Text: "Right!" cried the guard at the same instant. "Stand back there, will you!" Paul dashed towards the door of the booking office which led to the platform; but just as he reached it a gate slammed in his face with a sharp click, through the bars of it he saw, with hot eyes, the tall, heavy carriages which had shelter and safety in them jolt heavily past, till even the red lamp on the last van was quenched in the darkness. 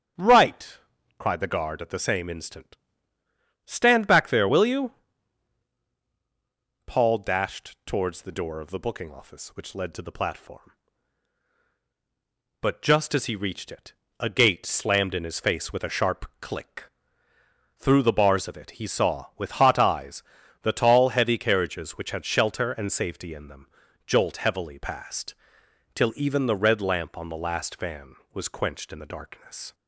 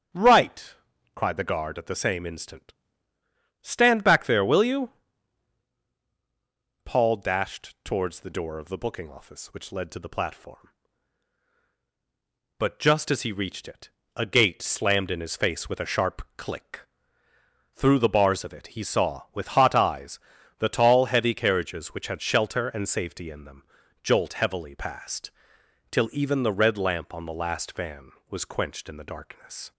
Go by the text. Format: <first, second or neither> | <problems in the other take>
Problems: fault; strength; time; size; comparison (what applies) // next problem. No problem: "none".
neither | starts louder than the rest; strong; the same in both // pauses between "it" and "a"; slight; the same in both // pauses between "them" and "jolt"; the same in both